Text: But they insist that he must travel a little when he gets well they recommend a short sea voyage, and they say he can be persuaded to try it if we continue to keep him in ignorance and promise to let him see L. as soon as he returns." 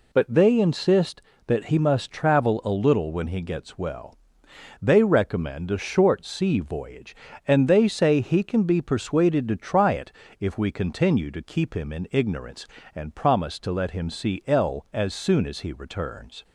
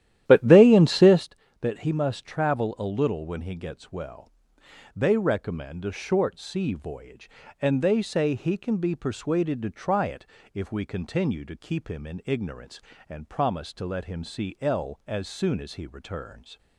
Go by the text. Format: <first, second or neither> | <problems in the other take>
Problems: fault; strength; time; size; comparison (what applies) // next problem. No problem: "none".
first | starts louder than the rest; strong; until 1.3 s; 12 dB // pauses between "well" and "they"; noticeable; at 4.2 s; 0.68 s long; noticeable in the first // pauses between "it" and "if"; slight; at 10.2 s; 0.28 s long; slight in the first